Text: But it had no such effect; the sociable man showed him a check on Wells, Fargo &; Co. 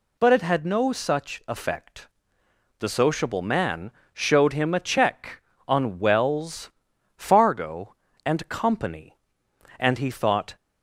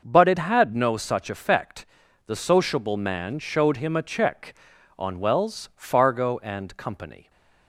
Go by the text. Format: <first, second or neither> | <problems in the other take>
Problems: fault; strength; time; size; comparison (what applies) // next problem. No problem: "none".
second | pauses between "man" and "showed"; slight; at 3.9 s; 0.22 s long // goes on to say "and he thought"; noticeable; from 9.7 s on; 0.78 s long